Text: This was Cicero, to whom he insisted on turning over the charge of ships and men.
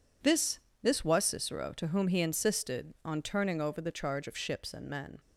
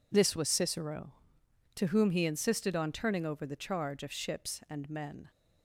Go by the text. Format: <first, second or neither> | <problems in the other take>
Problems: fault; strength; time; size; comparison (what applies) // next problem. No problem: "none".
second | says "This" twice; at 0.8 s